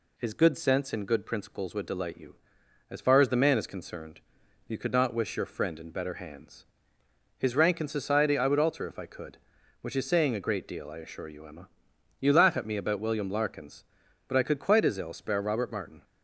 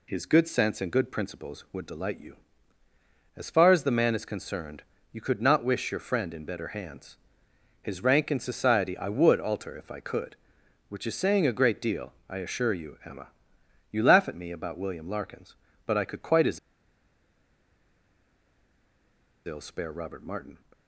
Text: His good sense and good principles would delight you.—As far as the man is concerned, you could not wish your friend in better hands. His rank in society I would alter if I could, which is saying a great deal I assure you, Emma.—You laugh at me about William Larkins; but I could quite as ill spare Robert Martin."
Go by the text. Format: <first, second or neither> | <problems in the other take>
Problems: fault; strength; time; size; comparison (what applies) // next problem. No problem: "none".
first | pauses between "deal" and "I"; slight; at 12.1 s; 0.16 s long // pauses between "as" and "ill"; strong; at 16.5 s; 2.8 s long